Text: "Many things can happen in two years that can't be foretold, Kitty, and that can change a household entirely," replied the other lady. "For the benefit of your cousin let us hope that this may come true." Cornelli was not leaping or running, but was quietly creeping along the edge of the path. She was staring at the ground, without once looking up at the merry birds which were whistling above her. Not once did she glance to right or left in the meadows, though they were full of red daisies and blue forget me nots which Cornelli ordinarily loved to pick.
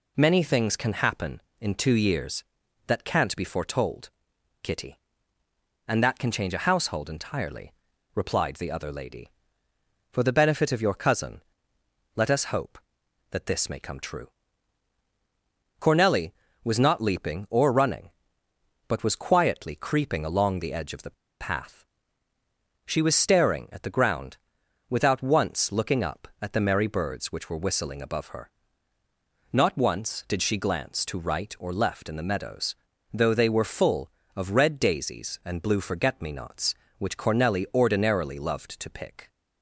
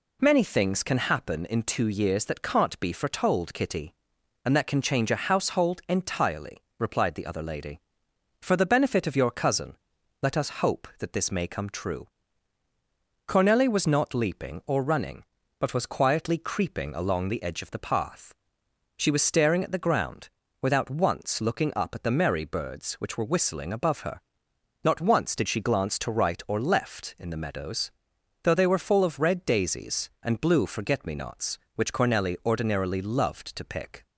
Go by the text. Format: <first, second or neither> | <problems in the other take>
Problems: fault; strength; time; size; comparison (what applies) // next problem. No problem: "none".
second | pauses between "cousin" and "let"; noticeable; at 11.4 s; 0.74 s long; noticeable in the second // pauses between "the" and "path"; slight; at 21.1 s; 0.28 s long